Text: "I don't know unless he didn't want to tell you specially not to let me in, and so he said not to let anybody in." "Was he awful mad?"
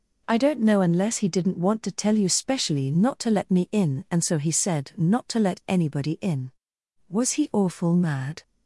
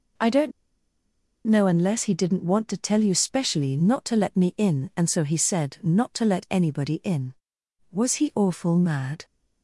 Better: first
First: none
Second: pauses between "don't" and "know"; noticeable; at 0.5 s; 0.95 s long

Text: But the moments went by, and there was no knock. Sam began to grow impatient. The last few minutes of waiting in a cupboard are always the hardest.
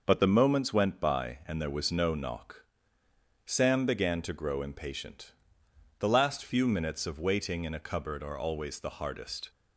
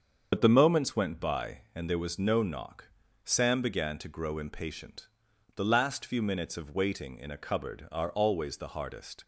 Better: first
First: none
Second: loses the start of "But"; at 0.3 s; 55 ms // starts louder than the rest; until 1.3 s; 7 dB

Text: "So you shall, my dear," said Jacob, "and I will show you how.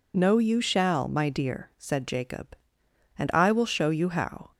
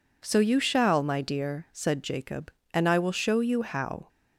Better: second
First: says "No" for "So"; at 0.1 s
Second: none

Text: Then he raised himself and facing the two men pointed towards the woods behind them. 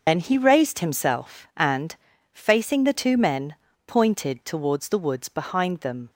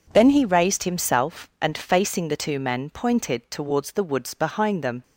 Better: second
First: loses the start of "Then"; at 0.0 s; 80 ms // pauses between "and" and "facing"; at 1.9 s; 0.38 s long // pauses between "men" and "pointed"; slight; at 3.5 s; 0.32 s long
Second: none

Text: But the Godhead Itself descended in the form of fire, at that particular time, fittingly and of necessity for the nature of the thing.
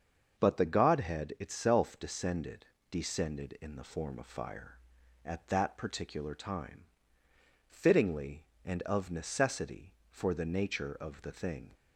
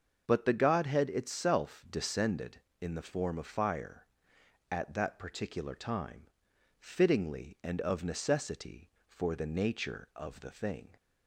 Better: second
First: starts louder than the rest; until 1.4 s; 6.5 dB // says "descended" twice; at 2.9 s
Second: starts louder than the rest; until 1.2 s; 6.5 dB

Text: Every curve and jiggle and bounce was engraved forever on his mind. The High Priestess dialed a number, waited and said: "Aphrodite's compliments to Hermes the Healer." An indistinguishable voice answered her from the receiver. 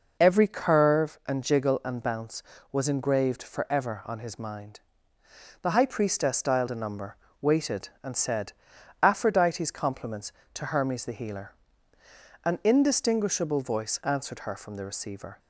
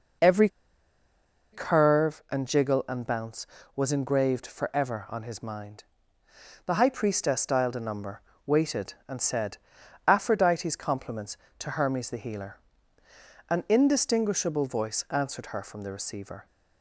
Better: first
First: none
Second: pauses between "Every" and "curve"; at 0.4 s; 1.0 s long

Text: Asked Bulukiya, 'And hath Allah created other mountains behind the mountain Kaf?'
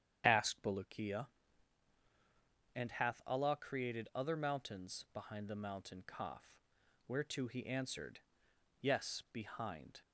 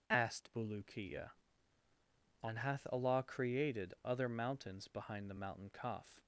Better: second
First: starts louder than the rest; strong; until 1.2 s; 9 dB // goes on to say "whereto he answered Yes behind"; strong; from 7.0 s on; 2.9 s long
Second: none

